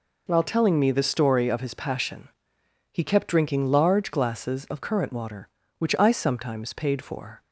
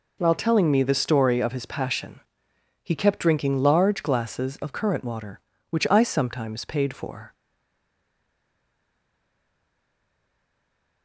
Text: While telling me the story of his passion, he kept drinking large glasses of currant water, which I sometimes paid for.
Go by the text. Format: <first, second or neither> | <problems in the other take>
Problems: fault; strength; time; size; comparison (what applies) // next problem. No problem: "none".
first | stays silent after the last word; strong; from 7.3 s on; 3.7 s long